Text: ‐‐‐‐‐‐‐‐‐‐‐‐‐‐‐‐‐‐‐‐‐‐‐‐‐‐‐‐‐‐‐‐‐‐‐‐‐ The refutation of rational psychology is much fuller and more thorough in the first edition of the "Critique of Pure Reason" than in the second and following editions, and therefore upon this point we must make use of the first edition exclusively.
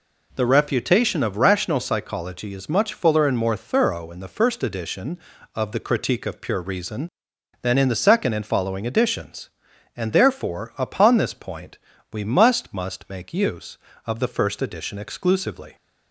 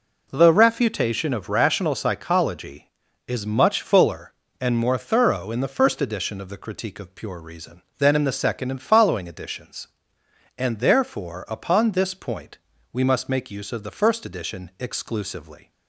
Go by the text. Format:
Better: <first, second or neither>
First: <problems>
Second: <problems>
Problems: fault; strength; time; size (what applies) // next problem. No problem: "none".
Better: second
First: pauses between "point" and "we"; slight; at 11.7 s; 0.36 s long // says "must" twice; at 12.7 s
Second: pauses between "point" and "we"; slight; at 12.5 s; 0.34 s long